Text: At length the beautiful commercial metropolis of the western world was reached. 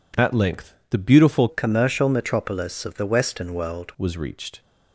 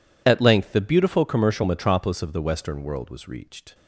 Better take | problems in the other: second | pauses between "length" and "the"; slight; at 0.7 s; 0.16 s long // changes voice from "commercial" to "world"; from 1.4 to 3.9 s; 2.5 s long

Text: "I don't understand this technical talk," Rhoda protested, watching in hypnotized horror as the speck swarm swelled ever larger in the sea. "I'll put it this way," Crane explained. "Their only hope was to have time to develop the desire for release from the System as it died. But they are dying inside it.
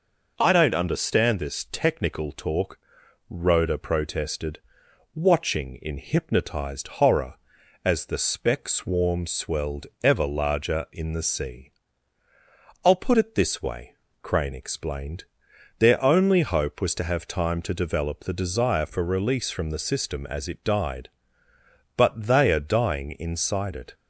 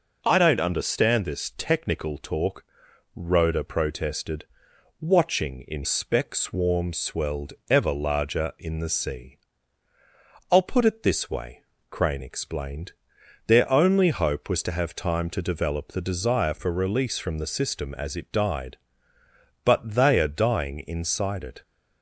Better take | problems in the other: first | skips "hypnotized horror as the"; at 5.8 s // pauses between "swelled" and "ever"; slight; at 7.5 s; 0.16 s long; slight in the first

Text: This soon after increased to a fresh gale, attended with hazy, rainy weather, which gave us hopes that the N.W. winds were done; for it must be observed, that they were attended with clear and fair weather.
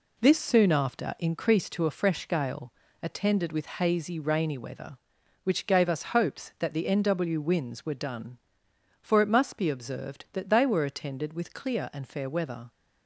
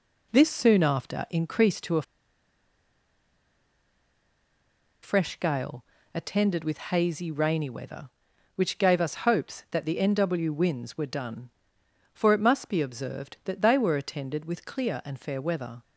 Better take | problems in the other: first | pauses between "a" and "fresh"; strong; at 2.0 s; 3.0 s long

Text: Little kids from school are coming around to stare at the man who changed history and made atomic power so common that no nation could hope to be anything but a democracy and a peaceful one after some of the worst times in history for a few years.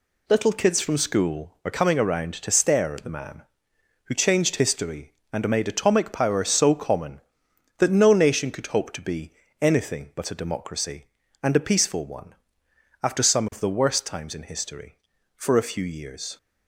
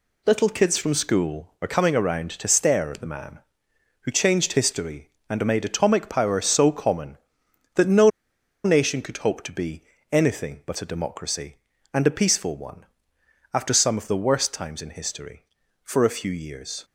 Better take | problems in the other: first | pauses between "no" and "nation"; noticeable; at 8.0 s; 0.55 s long // pauses between "be" and "anything"; slight; at 9.8 s; 0.30 s long; slight in the first // pauses between "one" and "after"; noticeable; at 12.8 s; 0.70 s long; noticeable in the first

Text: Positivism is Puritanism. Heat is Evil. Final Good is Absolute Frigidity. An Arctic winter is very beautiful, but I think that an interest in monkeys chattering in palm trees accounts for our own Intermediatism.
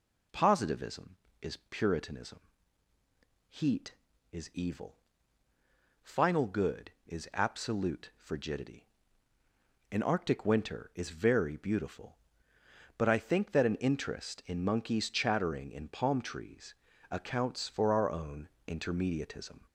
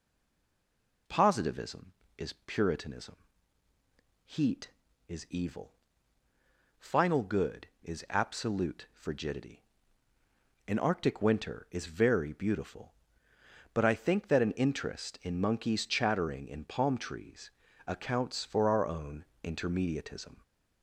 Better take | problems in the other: first | stays silent before the first word; until 1.0 s; 1.0 s long // pauses between "trees" and "accounts"; slight; at 17.5 s; 0.34 s long; slight in the first // pauses between "own" and "Intermediatism"; slight; at 19.2 s; 0.18 s long; slight in the first

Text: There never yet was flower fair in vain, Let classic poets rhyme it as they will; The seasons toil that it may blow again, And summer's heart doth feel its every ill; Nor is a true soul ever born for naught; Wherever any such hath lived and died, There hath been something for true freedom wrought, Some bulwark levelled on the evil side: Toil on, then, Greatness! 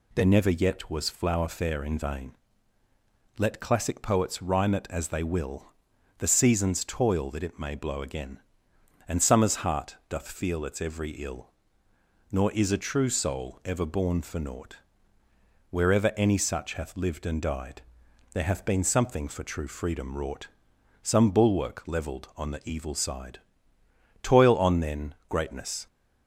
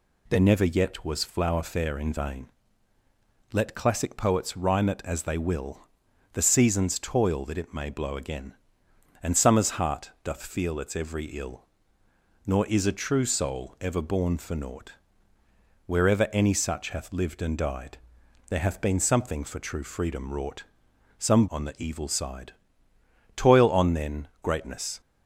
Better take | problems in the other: first | skips "bulwark levelled"; at 21.4 s

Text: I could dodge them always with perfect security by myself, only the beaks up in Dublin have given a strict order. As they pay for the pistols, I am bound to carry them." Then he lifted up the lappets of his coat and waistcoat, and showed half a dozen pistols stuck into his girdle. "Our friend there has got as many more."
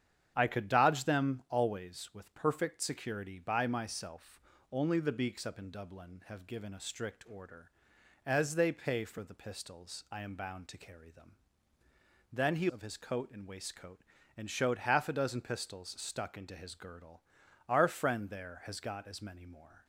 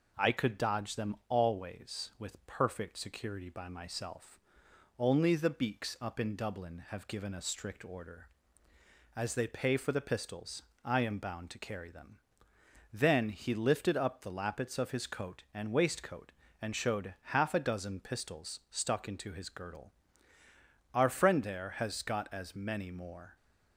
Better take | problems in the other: second | starts louder than the rest; strong; until 1.3 s; 8.5 dB // skips "lifted up the lappets"; at 12.6 s

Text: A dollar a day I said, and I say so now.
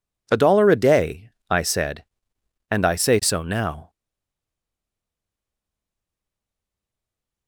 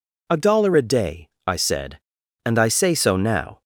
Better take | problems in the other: second | pauses between "day" and "I"; slight; at 1.3 s; 0.18 s long; slight in the second // stays silent after the last word; strong; from 3.8 s on; 3.6 s long

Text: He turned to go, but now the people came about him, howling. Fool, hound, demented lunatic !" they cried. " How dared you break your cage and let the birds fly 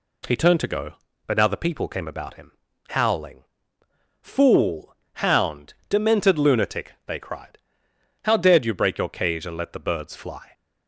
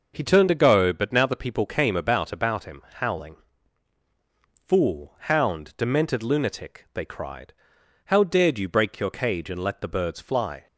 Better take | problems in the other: first | says "about" twice; at 2.3 s

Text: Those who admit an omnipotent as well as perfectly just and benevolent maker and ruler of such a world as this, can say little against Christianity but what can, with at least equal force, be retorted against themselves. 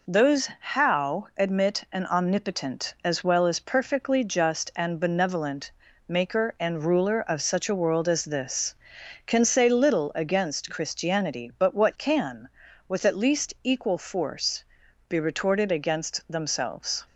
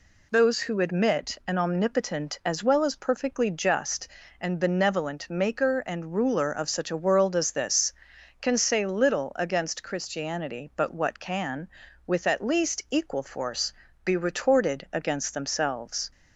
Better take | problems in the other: second | says "how" for "who"; at 0.5 s // pauses between "benevolent" and "maker"; at 5.6 s; 0.38 s long

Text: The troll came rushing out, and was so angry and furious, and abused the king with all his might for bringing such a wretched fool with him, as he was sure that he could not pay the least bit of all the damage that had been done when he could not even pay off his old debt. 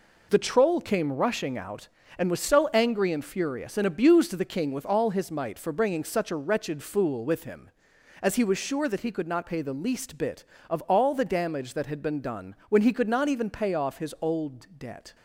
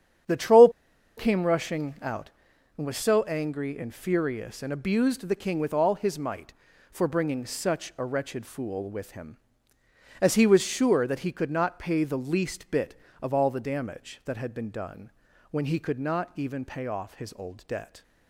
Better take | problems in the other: first | starts louder than the rest; strong; until 1.7 s; 9 dB // pauses between "troll" and "came"; noticeable; at 0.6 s; 0.48 s long // pauses between "done" and "when"; at 15.1 s; 0.40 s long

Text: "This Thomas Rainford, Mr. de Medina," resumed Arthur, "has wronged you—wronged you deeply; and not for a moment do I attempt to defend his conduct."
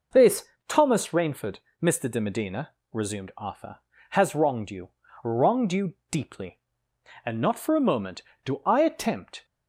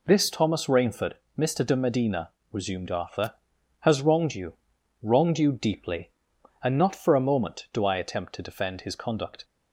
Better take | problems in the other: second | pauses between "This" and "Thomas"; slight; at 0.4 s; 0.22 s long // pauses between "you" and "deeply"; slight; at 5.9 s; 0.18 s long // stops before "to defend his conduct"; at 9.4 s

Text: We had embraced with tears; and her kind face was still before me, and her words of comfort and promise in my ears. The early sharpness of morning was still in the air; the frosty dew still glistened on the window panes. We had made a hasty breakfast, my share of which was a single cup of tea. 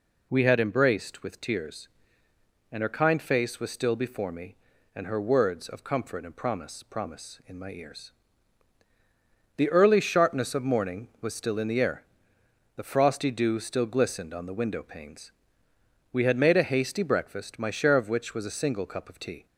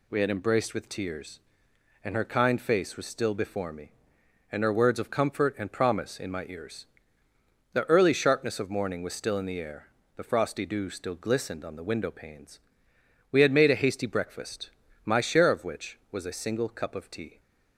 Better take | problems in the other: second | says "promise" twice; at 6.8 s

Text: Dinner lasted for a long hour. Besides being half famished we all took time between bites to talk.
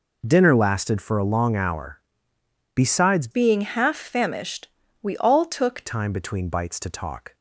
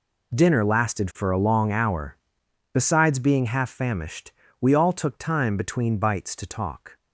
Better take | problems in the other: second | changes voice from "being" to "took"; from 3.3 to 5.8 s; 2.5 s long // pauses between "famished" and "we"; at 4.6 s; 0.38 s long; slight in the second

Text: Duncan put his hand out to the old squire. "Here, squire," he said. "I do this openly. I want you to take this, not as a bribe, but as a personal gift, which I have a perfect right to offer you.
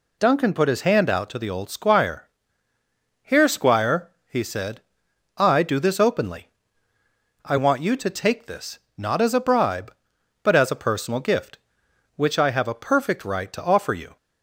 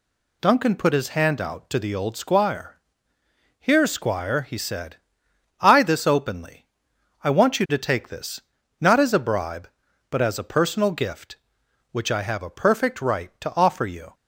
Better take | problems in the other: first | skips "do"; at 5.8 s

